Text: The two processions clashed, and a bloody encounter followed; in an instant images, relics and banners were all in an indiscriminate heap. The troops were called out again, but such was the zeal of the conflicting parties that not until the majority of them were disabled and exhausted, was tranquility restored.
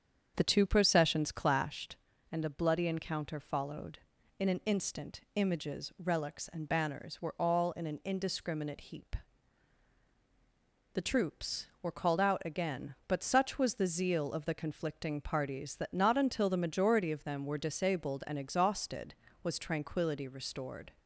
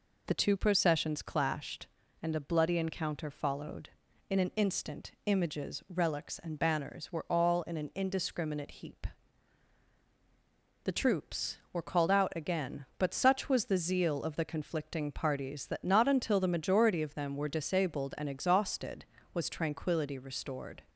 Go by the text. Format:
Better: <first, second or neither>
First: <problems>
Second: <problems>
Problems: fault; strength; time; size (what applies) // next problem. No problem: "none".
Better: second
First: starts louder than the rest; strong; until 1.7 s; 7.5 dB // pauses between "instant" and "images"; slight; at 5.2 s; 0.16 s long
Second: pauses between "instant" and "images"; slight; at 5.1 s; 0.16 s long